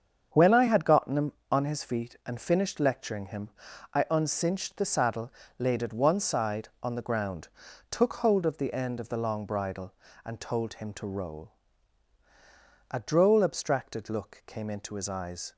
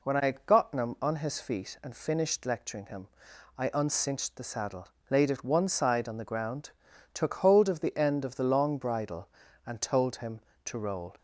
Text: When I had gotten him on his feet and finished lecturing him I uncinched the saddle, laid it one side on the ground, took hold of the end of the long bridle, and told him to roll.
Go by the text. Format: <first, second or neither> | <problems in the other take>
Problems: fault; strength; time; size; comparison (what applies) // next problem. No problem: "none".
second | starts louder than the rest; strong; until 1.5 s; 7.5 dB // pauses between "him" and "I"; noticeable; at 3.4 s; 0.46 s long; noticeable in the second // goes on to say "A droll abstracted look came into his eyes"; strong; from 12.9 s on; 2.6 s long